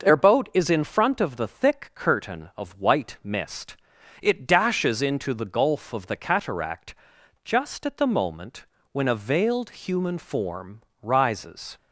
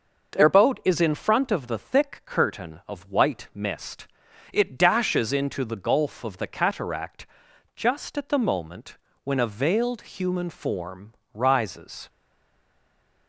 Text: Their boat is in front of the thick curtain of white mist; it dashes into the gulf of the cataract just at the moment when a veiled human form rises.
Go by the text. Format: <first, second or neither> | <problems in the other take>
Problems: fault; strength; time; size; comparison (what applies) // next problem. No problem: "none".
first | pauses between "cataract" and "just"; noticeable; at 7.2 s; 0.50 s long; noticeable in the first // pauses between "moment" and "when"; slight; at 8.9 s; 0.28 s long; slight in the first // pauses between "form" and "rises"; slight; at 11.1 s; 0.22 s long; slight in the first // stays silent after the last word; noticeable; from 12.0 s on; 1.2 s long